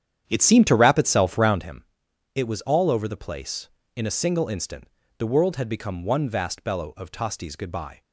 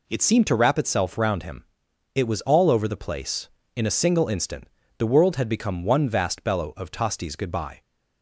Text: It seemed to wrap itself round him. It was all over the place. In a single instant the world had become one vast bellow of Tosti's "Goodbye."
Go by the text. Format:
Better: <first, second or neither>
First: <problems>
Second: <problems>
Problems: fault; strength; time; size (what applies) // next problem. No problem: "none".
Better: second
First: starts louder than the rest; strong; until 1.7 s; 9.5 dB // pauses between "instant" and "the"; slight; at 4.8 s; 0.32 s long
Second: pauses between "instant" and "the"; slight; at 4.6 s; 0.32 s long